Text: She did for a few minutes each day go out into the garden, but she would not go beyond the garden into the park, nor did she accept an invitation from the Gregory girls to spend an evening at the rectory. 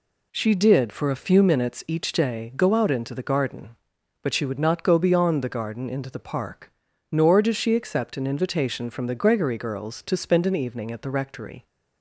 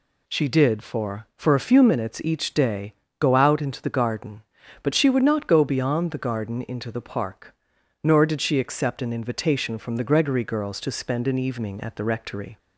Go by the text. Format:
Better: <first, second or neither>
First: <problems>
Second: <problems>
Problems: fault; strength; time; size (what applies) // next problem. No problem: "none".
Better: first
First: none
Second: says "for" twice; at 1.3 s // pauses between "day" and "go"; slight; at 2.9 s; 0.26 s long